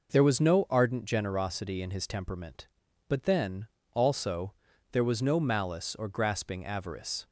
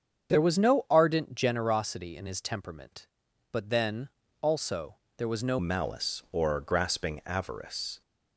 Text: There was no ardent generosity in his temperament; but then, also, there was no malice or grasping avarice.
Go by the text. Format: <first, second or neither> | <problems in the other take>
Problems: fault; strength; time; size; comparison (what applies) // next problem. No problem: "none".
first | starts louder than the rest; strong; until 1.3 s; 7.5 dB // changes voice at "malice"; from 5.5 s on; 2.5 s long